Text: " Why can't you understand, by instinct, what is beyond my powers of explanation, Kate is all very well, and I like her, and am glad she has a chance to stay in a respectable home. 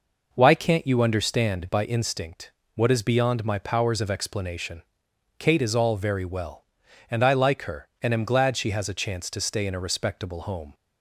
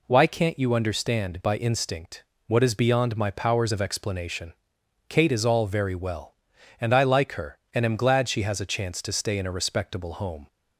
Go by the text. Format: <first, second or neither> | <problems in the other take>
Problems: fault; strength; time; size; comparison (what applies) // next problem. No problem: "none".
second | starts louder than the rest; noticeable; until 1.8 s; 5 dB